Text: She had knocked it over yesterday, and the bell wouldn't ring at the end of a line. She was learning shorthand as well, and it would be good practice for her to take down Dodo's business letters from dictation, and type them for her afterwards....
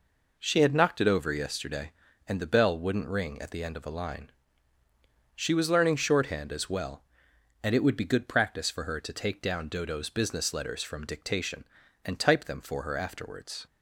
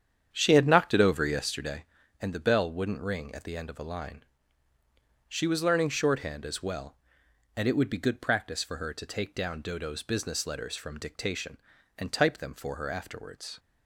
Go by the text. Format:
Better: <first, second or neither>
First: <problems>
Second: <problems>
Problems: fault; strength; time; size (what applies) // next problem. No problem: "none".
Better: first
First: none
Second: starts louder than the rest; strong; until 1.8 s; 8.5 dB